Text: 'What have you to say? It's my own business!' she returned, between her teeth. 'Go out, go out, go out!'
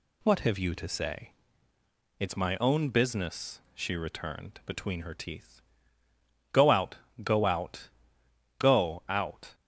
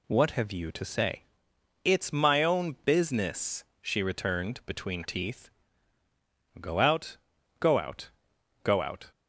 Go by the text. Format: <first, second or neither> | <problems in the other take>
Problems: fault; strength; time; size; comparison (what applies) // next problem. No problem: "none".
first | skips "her"; at 5.0 s